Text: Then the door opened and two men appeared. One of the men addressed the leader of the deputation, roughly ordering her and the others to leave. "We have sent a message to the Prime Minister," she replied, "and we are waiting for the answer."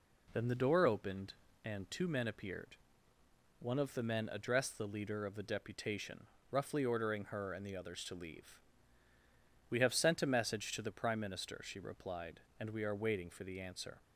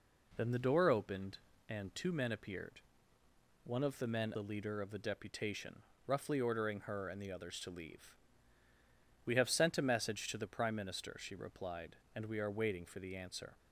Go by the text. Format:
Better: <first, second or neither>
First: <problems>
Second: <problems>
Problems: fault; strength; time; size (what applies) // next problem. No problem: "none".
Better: first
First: none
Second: skips "addressed"; at 4.3 s